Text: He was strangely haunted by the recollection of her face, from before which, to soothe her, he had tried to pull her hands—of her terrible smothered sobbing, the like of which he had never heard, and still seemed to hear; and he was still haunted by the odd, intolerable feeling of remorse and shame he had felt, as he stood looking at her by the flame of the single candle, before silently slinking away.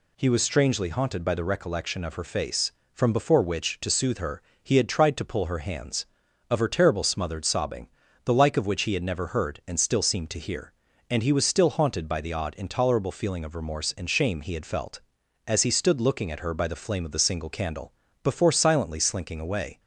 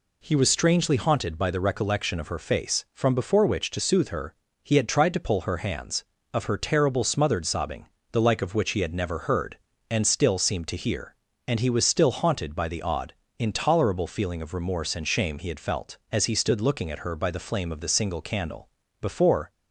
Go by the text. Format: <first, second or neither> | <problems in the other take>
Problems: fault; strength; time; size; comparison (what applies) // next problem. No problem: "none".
first | stops before "silently slinking away"; at 19.5 s